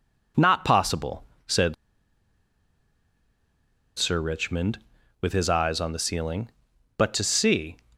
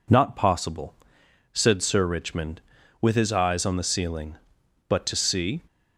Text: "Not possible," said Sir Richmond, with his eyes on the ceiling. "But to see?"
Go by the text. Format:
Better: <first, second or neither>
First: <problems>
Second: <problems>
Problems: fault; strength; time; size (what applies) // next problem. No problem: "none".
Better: second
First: pauses between "said" and "Sir"; strong; at 1.7 s; 2.2 s long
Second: none